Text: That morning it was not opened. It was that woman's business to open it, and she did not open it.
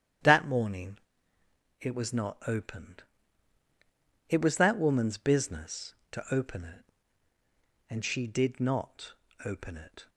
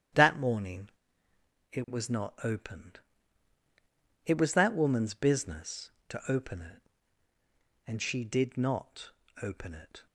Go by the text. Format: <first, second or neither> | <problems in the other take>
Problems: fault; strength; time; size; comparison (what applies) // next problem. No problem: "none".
neither | starts louder than the rest; strong; the same in both // pauses between "morning" and "it"; noticeable; the same in both // pauses between "not" and "open"; slight; the same in both